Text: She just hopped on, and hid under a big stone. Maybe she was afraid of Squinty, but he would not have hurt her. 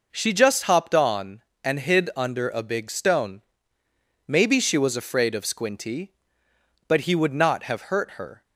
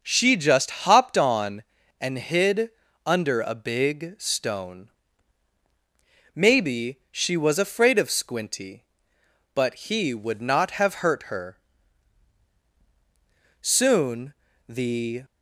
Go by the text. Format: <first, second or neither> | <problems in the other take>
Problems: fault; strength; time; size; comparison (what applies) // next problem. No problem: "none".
first | starts louder than the rest; noticeable; until 1.0 s; 6 dB // pauses between "hid" and "under"; at 2.6 s; 0.38 s long // goes on to say "Soon the"; from 13.6 s on; 1.6 s long